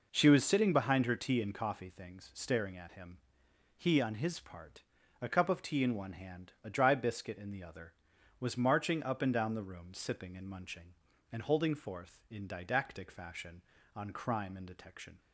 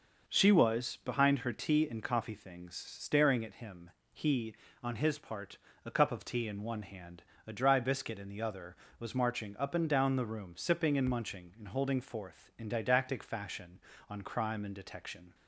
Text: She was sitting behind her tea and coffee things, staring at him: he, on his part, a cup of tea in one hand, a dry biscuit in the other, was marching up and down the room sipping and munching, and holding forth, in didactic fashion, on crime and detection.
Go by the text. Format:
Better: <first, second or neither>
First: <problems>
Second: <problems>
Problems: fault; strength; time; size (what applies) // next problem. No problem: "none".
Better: first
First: none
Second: starts louder than the rest; noticeable; until 1.3 s; 6 dB // skips "sitting"; at 1.0 s